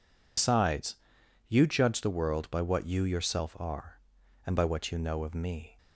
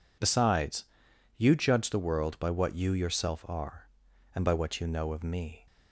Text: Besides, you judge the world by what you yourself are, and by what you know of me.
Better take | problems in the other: second | loses the start of "Besides"; at 0.3 s; 60 ms

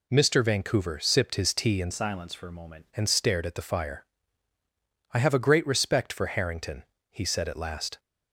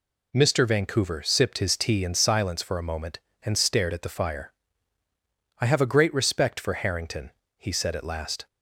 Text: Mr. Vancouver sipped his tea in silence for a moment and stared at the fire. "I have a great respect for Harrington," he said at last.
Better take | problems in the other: second | changes voice from "silence" to "moment"; from 1.9 to 2.8 s; 0.9 s long

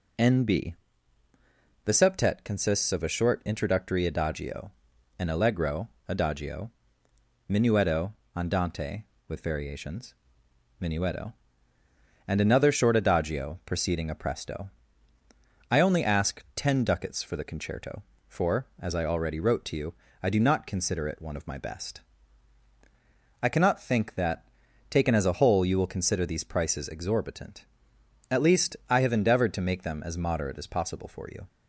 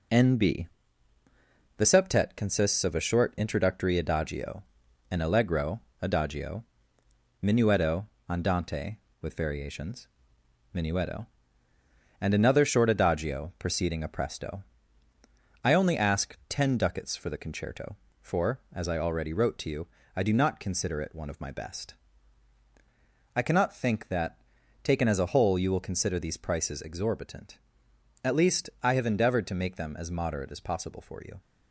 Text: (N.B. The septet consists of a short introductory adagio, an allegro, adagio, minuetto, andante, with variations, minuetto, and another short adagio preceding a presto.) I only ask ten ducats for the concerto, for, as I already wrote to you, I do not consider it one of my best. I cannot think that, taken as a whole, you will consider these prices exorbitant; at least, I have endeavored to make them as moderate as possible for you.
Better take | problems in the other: first | gets quieter; noticeable; throughout; 6 dB

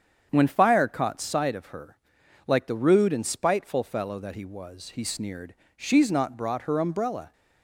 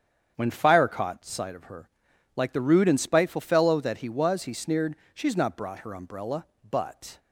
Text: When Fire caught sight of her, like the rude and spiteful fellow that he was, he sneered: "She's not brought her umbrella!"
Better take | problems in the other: first | starts louder than the rest; strong; until 1.3 s; 8 dB; strong in the first // goes on to say "But"; from 6.6 s on; 0.50 s long

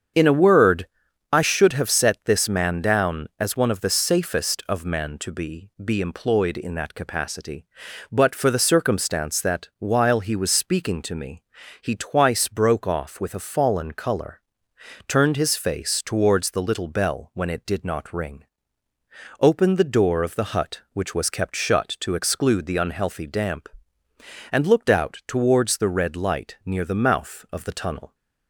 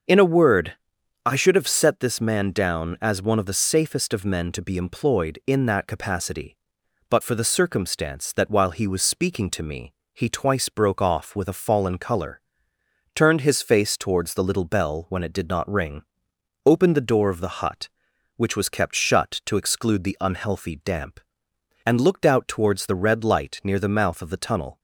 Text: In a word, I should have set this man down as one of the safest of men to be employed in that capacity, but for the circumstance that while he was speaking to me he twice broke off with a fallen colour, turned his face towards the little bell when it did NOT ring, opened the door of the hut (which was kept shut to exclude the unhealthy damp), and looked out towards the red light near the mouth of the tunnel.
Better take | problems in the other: second | starts louder than the rest; strong; until 1.6 s; 7 dB; also in the second // says "be" twice; at 5.8 s // pauses between "me" and "he"; at 11.4 s; 0.40 s long; slight in the second

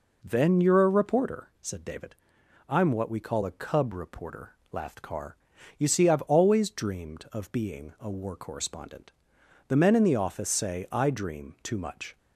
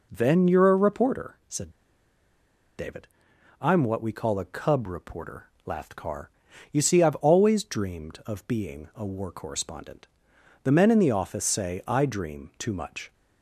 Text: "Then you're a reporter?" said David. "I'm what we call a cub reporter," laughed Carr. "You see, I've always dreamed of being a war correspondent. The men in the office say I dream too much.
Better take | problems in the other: first | pauses between "said" and "David"; at 1.6 s; 1.0 s long

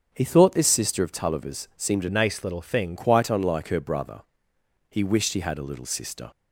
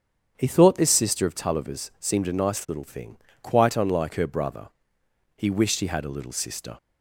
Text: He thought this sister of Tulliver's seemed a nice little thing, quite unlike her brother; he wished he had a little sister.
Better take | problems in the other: second | starts louder than the rest; strong; until 1.1 s; 7.5 dB; strong in the second // changes voice from "nice" to "thing"; from 2.0 to 2.9 s; 0.9 s long

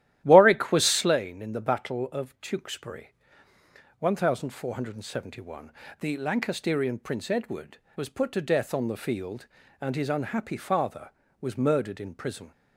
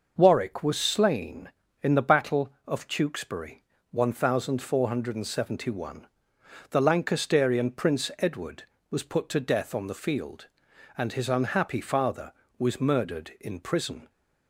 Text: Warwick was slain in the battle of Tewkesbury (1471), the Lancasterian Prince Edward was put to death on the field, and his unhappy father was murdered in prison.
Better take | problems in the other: second | starts louder than the rest; strong; until 1.2 s; 13 dB

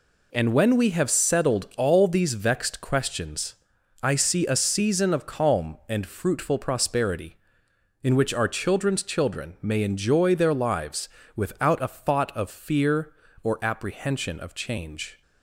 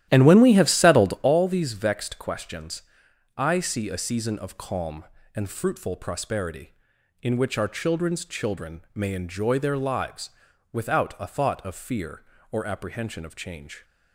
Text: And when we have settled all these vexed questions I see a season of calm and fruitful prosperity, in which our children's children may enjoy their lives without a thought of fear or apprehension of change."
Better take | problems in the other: first | starts louder than the rest; strong; until 1.3 s; 12.5 dB // pauses between "questions" and "I"; noticeable; at 2.8 s; 0.54 s long; noticeable in the first // pauses between "children" and "may"; slight; at 8.7 s; 0.16 s long // pauses between "lives" and "without"; at 10.2 s; 0.42 s long; slight in the first

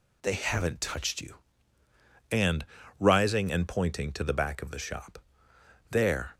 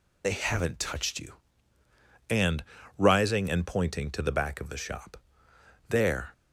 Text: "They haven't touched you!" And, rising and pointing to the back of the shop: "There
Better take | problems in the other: first | loses the start of "They"; at 0.2 s; 40 ms

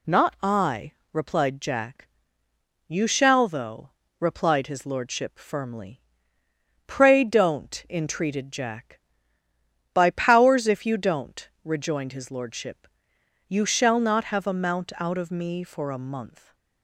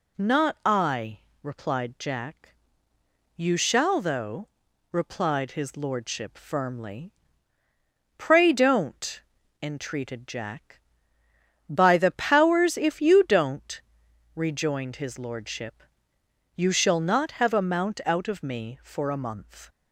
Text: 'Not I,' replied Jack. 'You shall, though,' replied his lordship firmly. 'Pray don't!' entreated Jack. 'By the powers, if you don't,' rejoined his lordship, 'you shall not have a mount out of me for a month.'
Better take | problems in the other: second | skips "the"; at 10.1 s

